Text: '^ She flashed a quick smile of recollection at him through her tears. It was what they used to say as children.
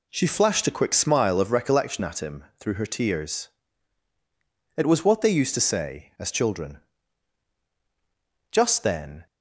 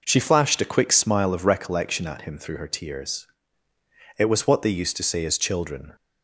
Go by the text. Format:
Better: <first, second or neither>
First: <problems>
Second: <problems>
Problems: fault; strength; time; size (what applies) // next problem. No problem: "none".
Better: second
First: goes on to say "Just then"; noticeable; from 8.4 s on; 0.76 s long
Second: none